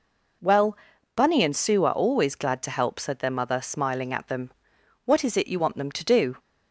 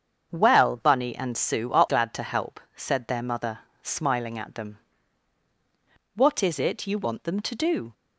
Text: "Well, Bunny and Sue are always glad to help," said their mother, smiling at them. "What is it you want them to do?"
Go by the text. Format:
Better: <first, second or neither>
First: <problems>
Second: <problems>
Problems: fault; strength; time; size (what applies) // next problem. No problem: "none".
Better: first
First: none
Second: starts louder than the rest; strong; until 1.3 s; 7.5 dB // skips "always"; at 1.8 s